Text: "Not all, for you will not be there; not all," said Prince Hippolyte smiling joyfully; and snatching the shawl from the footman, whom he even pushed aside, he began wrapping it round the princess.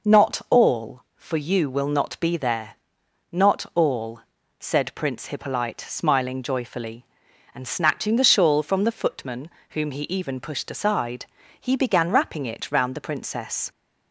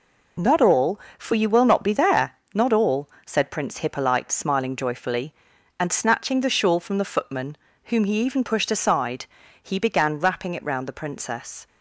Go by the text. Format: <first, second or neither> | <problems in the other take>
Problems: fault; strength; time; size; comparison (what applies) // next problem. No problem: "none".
neither | none